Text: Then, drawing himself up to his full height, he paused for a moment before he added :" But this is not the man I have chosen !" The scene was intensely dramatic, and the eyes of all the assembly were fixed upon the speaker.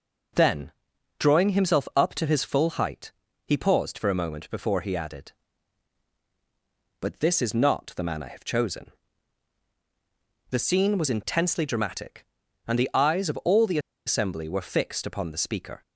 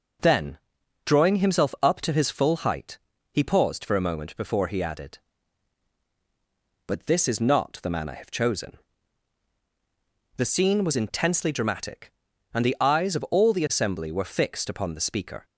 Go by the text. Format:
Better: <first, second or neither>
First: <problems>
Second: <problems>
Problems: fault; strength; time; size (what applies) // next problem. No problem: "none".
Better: second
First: starts louder than the rest; strong; until 1.8 s; 8 dB // pauses between "the" and "assembly"; slight; at 13.7 s; 0.28 s long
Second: starts louder than the rest; strong; until 1.6 s; 8 dB